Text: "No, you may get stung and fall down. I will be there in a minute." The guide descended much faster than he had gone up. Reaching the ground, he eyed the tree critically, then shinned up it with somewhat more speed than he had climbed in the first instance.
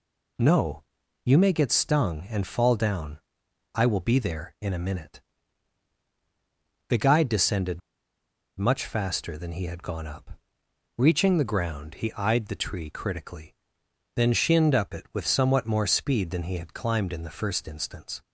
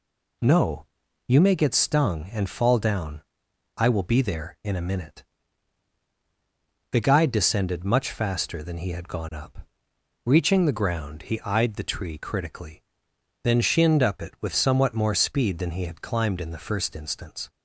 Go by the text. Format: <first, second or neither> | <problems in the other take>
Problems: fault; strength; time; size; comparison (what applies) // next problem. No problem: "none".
second | pauses between "descended" and "much"; noticeable; at 7.8 s; 0.79 s long